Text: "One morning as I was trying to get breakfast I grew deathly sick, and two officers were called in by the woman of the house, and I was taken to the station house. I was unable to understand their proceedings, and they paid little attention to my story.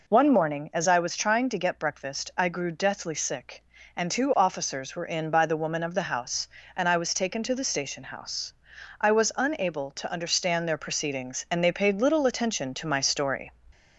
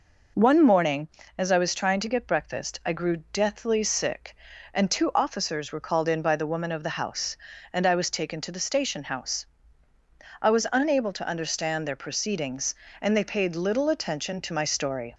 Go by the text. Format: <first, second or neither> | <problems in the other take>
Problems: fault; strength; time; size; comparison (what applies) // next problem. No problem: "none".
second | skips "called"; at 5.0 s